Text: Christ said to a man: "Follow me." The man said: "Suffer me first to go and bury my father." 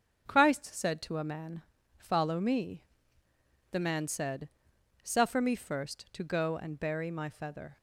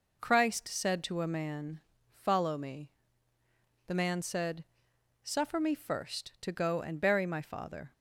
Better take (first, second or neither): second